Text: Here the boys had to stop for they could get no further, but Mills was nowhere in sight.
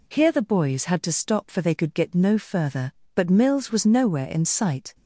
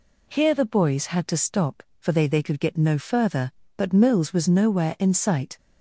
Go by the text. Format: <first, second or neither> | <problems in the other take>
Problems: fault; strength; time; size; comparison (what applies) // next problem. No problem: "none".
first | says "they" twice; at 2.2 s